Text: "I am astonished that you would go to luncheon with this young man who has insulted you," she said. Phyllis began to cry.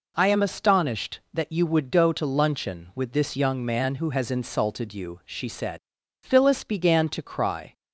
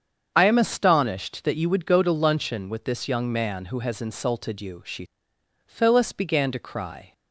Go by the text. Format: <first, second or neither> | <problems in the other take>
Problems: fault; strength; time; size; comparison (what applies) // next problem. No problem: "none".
first | starts louder than the rest; until 1.3 s; 7 dB // skips "said"; at 5.3 s